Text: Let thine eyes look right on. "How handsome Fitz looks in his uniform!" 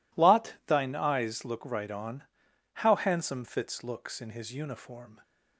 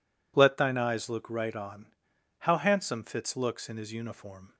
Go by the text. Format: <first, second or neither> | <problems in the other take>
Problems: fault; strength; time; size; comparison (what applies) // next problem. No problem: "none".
second | says "Lot" for "Let"; at 0.1 s